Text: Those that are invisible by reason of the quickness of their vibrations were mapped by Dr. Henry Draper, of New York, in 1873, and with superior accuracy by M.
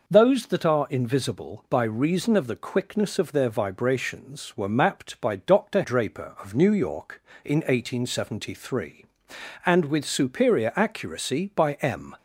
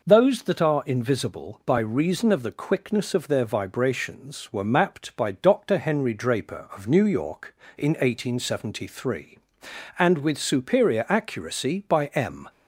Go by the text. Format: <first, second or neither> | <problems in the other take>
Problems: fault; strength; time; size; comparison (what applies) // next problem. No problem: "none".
second | skips "Henry"; at 5.8 s